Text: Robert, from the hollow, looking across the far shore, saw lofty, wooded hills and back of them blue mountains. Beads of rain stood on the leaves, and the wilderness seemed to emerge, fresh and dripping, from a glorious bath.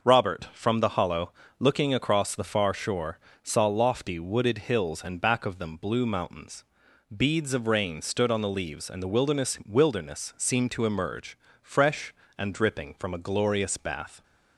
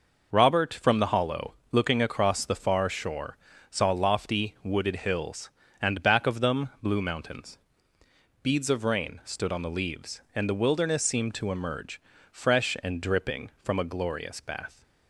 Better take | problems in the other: second | starts louder than the rest; until 1.0 s; 6 dB // says "wilderness" twice; at 9.6 s

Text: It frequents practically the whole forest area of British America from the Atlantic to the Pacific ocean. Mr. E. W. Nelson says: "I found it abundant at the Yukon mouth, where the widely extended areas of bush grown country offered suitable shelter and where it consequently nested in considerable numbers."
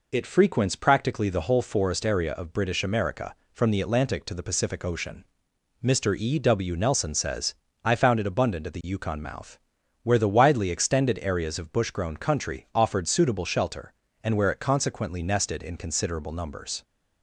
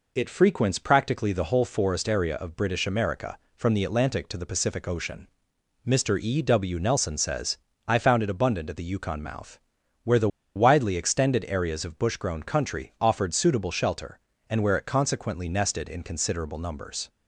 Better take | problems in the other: first | pauses between "the" and "widely"; slight; at 10.2 s; 0.27 s long

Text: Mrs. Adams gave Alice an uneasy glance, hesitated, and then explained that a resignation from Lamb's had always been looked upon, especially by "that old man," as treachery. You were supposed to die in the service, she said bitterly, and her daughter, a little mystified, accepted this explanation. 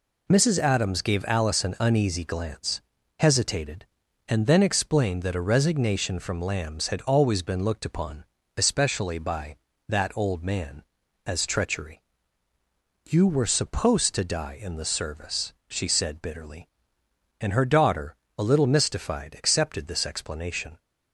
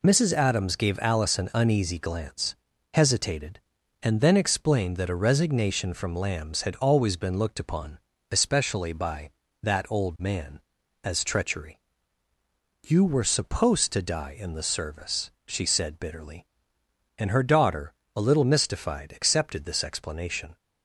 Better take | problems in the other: neither | none

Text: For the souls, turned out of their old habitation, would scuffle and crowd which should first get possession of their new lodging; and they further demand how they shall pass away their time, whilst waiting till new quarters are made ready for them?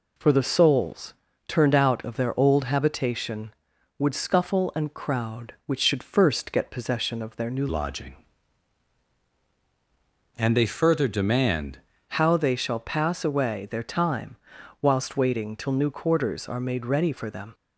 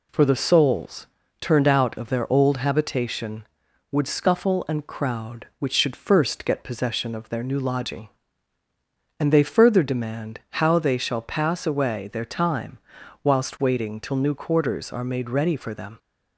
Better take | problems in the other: second | changes voice from "lodging" to "demand"; from 7.6 to 11.7 s; 4.1 s long

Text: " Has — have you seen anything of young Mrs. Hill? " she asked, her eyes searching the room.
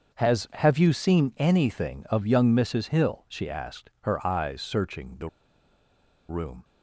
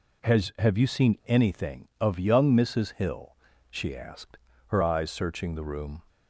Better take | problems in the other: second | starts louder than the rest; until 1.2 s; 6.5 dB // pauses between "the" and "room"; at 5.2 s; 1.0 s long

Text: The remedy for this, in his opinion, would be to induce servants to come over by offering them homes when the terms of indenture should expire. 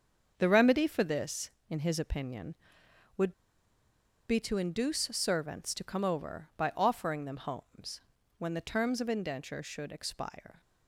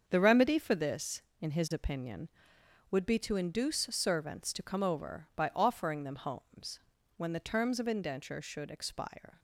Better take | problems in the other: second | starts louder than the rest; until 1.3 s; 7 dB; also in the second // pauses between "would" and "be"; noticeable; at 3.3 s; 0.97 s long // pauses between "homes" and "when"; at 8.0 s; 0.38 s long; also in the second

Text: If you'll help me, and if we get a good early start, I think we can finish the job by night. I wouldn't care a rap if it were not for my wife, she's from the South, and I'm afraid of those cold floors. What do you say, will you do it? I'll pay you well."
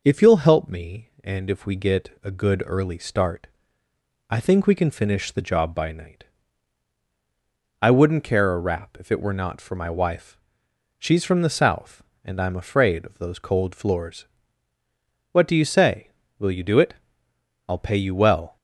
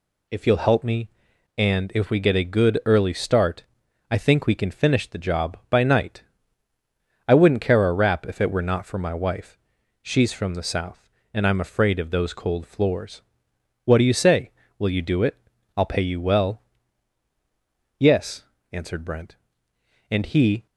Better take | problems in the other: first | goes on to say "Yes answered Brent and he"; strong; from 17.9 s on; 2.6 s long

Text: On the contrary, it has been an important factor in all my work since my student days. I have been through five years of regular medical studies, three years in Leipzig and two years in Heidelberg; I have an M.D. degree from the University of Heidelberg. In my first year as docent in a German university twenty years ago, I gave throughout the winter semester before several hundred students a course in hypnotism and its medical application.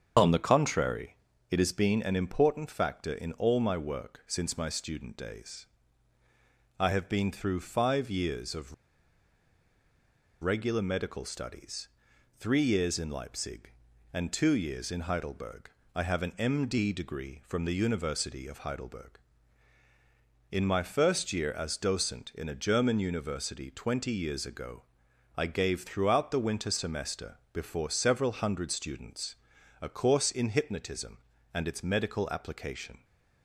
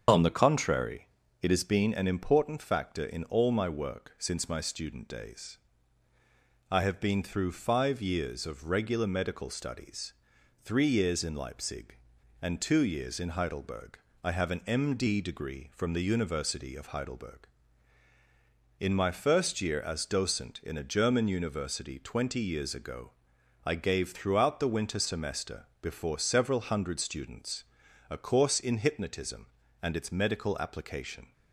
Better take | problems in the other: second | starts louder than the rest; until 1.5 s; 7 dB; also in the second // pauses between "of" and "regular"; strong; at 8.7 s; 1.6 s long // pauses between "semester" and "before"; slight; at 27.3 s; 0.16 s long; slight in the second // pauses between "students" and "a"; noticeable; at 29.3 s; 0.48 s long; noticeable in the second

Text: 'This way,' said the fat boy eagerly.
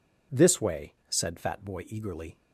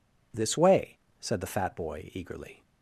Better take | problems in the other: second | skips "the"; at 1.3 s

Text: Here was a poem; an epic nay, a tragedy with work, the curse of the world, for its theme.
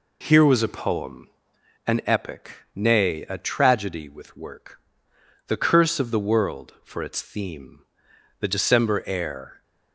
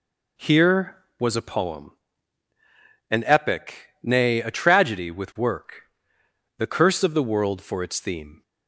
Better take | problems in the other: second | pauses between "epic" and "nay"; slight; at 2.5 s; 0.24 s long; slight in the second // goes on to say "The December air"; noticeable; from 8.3 s on; 1.2 s long

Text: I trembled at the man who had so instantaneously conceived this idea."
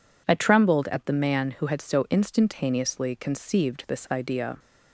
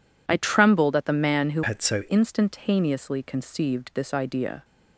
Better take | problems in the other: first | changes voice from "had" to "so"; from 1.6 to 2.0 s; 0.4 s long

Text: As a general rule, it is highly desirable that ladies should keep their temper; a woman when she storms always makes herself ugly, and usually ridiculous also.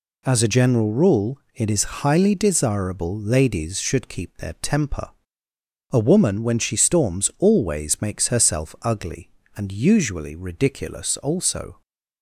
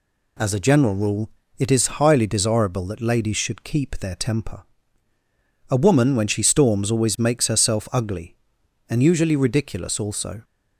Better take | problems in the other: second | skips "that"; at 3.1 s

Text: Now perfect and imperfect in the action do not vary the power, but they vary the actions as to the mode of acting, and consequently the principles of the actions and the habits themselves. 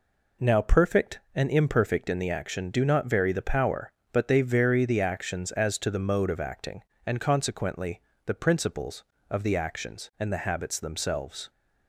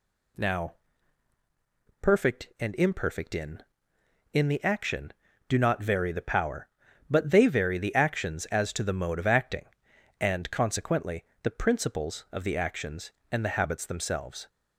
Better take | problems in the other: first | pauses between "Now" and "perfect"; strong; at 0.7 s; 1.2 s long // says "in" twice; at 4.3 s // pauses between "consequently" and "the"; slight; at 11.2 s; 0.18 s long; slight in the first

